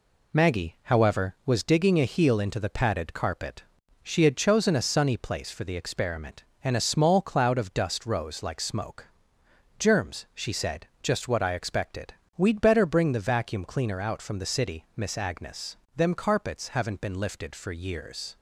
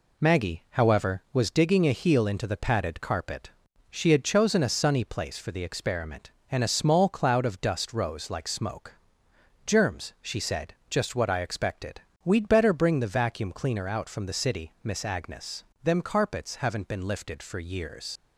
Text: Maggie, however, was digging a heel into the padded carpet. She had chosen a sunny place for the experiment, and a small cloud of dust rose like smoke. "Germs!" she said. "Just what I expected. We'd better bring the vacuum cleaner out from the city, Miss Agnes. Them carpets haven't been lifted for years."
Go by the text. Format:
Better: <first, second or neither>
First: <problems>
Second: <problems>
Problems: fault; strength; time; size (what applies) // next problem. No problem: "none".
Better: first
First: none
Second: leaves "years" unfinished; at 18.1 s; 80 ms